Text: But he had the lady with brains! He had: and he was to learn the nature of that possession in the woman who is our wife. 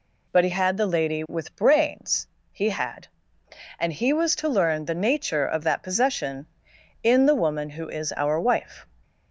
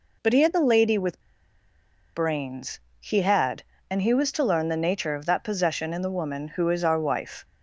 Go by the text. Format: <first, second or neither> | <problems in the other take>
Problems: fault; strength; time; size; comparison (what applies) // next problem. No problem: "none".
first | pauses between "with" and "brains"; noticeable; at 1.2 s; 0.92 s long